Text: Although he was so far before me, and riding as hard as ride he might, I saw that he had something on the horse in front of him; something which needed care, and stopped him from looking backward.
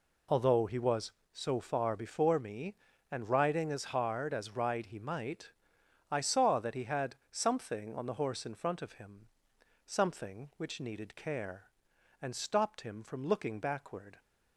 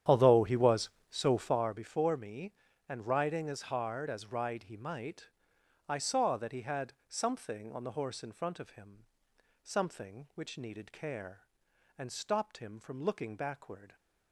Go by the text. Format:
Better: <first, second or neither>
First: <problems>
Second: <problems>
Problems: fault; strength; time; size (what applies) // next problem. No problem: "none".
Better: first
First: none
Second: starts louder than the rest; strong; until 1.7 s; 10 dB